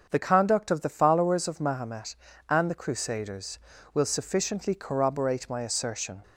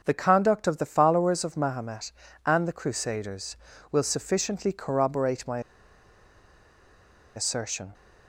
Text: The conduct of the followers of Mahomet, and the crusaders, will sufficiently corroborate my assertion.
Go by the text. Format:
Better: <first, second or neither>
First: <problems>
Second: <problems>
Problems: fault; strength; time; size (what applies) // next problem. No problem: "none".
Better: first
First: starts louder than the rest; until 1.1 s; 7 dB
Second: starts louder than the rest; until 1.0 s; 6.5 dB // pauses between "my" and "assertion"; strong; at 5.5 s; 1.7 s long